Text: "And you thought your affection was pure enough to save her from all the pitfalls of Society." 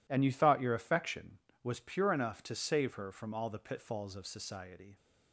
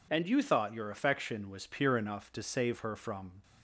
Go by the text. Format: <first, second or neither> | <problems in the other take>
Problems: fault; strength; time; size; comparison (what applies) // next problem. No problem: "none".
first | stops before "all the pitfalls of Society"; at 3.4 s